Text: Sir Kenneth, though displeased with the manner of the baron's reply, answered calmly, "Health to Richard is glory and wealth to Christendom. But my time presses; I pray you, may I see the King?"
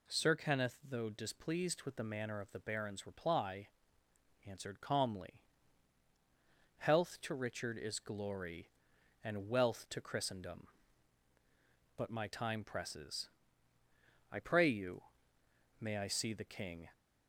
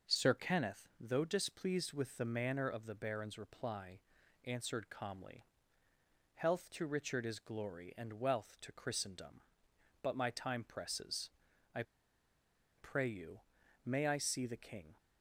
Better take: first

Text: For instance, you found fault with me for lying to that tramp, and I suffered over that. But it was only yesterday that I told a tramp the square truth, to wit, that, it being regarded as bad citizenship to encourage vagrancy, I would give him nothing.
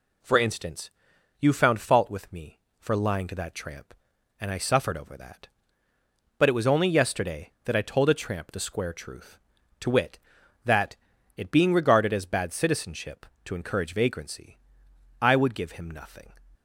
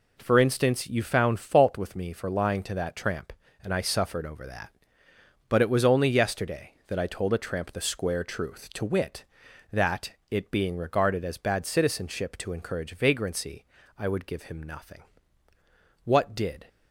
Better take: first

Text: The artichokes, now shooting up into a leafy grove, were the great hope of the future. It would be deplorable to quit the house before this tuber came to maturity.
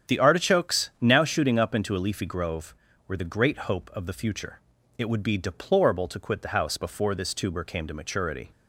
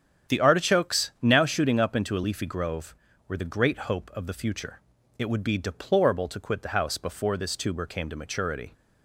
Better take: neither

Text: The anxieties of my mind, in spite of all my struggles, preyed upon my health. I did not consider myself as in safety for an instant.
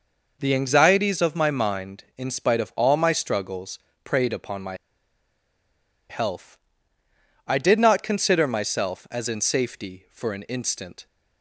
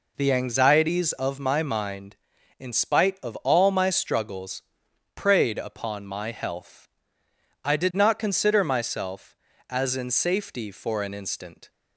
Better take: second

